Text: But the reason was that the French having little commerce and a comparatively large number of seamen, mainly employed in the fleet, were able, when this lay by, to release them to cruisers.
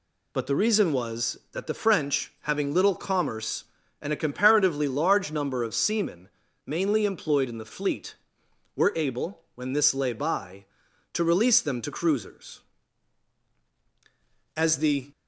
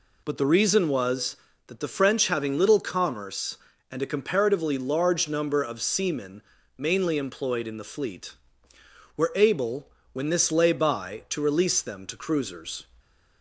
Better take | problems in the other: second | goes on to say "As the"; from 14.5 s on; 0.54 s long

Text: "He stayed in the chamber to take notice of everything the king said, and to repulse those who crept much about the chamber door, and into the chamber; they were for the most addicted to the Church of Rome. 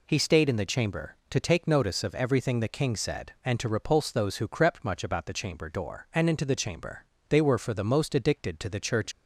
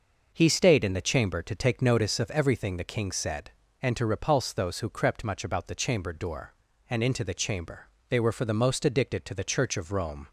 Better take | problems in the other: second | stops before "of Rome"; at 9.1 s

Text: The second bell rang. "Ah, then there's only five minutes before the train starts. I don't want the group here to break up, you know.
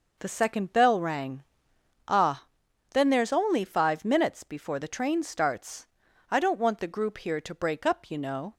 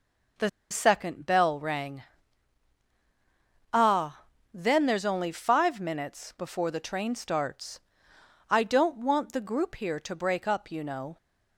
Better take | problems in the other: first | pauses between "The" and "second"; slight; at 0.4 s; 0.21 s long

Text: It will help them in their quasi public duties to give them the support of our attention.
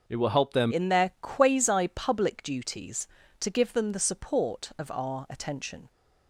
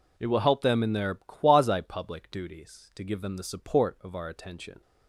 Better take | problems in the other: second | starts louder than the rest; until 1.0 s; 6 dB // changes voice at "in"; from 0.7 s on; 5.1 s long

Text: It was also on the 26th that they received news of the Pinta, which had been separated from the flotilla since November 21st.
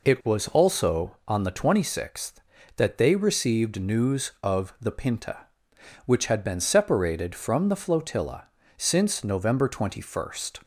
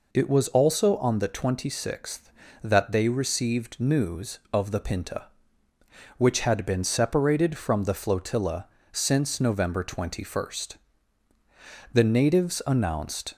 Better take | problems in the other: first | pauses between "flotilla" and "since"; slight; at 8.6 s; 0.24 s long; slight in the first // goes on to say "The natives announced"; from 11.9 s on; 1.4 s long

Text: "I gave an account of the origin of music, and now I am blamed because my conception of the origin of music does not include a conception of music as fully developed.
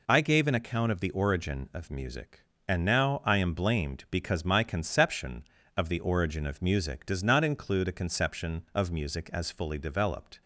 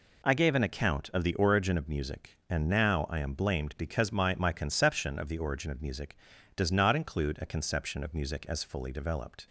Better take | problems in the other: first | says "my" twice; at 4.3 s

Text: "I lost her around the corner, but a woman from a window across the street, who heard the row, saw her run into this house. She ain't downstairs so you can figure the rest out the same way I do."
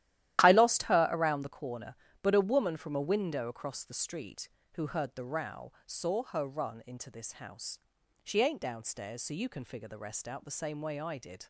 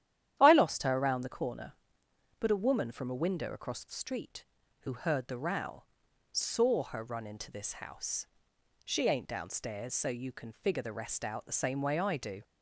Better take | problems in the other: second | starts louder than the rest; strong; until 1.4 s; 13 dB; strong in the second // says "did" for "do"; at 11.1 s

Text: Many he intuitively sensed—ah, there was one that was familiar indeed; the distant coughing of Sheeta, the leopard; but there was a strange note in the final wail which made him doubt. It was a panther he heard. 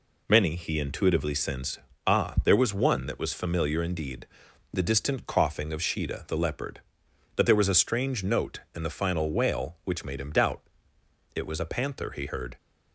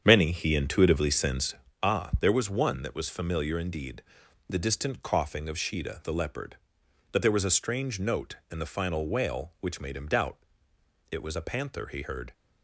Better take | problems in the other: first | starts louder than the rest; strong; until 1.8 s; 8 dB

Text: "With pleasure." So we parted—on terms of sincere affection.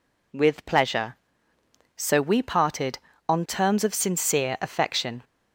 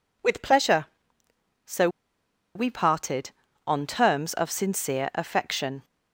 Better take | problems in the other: first | pauses between "So" and "we"; noticeable; at 1.8 s; 0.67 s long

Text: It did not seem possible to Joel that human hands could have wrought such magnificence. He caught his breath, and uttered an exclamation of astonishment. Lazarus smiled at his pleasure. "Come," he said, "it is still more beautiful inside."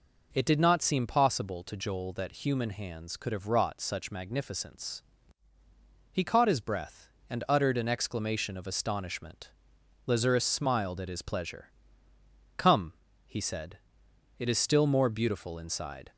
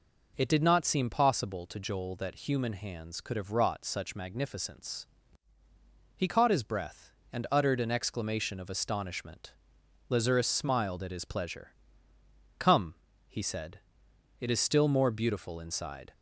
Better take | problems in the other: neither | none

